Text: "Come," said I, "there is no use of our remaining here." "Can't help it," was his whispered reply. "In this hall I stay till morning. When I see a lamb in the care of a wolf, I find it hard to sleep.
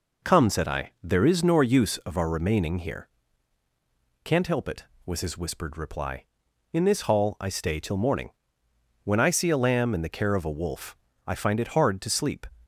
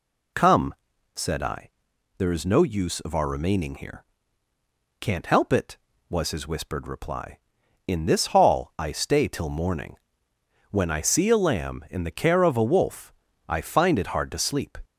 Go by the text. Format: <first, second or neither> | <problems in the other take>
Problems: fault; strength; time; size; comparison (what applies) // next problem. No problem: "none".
second | says "nor" for "no"; at 1.4 s